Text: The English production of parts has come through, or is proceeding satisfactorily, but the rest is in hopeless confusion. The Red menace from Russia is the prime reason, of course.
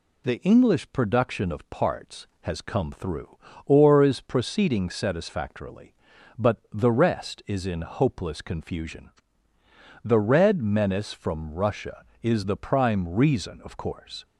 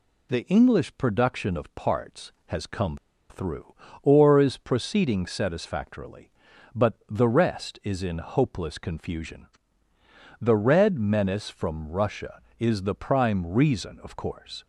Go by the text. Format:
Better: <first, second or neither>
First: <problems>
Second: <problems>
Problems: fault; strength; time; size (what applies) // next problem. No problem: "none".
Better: first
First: pauses between "but" and "the"; slight; at 6.5 s; 0.16 s long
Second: pauses between "come" and "through"; slight; at 2.9 s; 0.33 s long // pauses between "but" and "the"; slight; at 6.9 s; 0.16 s long